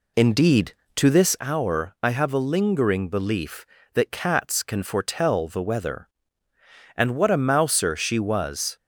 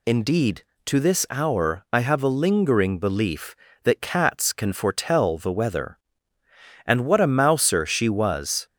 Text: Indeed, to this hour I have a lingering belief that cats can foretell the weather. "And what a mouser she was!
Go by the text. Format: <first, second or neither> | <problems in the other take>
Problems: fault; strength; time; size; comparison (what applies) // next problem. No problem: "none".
second | starts louder than the rest; slight; until 1.4 s; 2.5 dB